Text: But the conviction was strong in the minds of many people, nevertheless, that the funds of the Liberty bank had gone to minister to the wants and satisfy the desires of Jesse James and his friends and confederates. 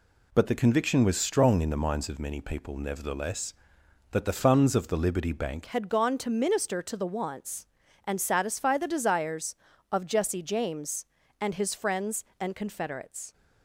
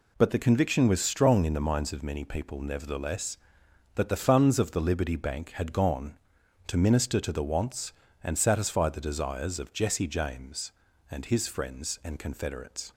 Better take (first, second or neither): second